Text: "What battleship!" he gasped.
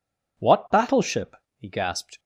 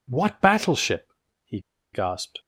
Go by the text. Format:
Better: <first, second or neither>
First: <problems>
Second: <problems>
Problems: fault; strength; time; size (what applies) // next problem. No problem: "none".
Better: first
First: none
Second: pauses between "he" and "gasped"; slight; at 1.6 s; 0.32 s long